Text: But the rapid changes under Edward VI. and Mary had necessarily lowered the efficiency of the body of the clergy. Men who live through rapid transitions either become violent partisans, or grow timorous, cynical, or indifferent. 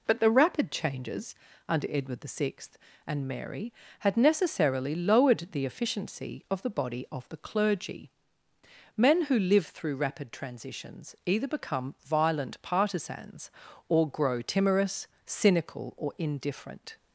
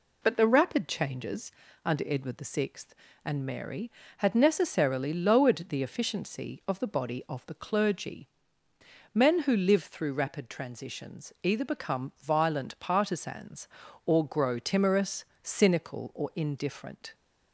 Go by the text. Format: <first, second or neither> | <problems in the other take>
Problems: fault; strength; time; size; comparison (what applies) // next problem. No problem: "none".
neither | pauses between "changes" and "under"; slight; the same in both